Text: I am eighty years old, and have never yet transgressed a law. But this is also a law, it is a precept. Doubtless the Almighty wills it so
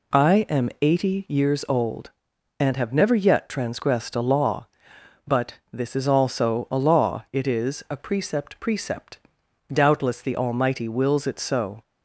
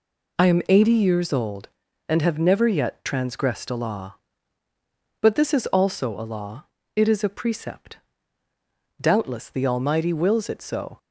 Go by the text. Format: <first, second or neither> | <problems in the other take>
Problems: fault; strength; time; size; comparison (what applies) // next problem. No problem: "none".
second | pauses between "But" and "this"; slight; at 5.5 s; 0.18 s long // says "precept" twice; at 8.6 s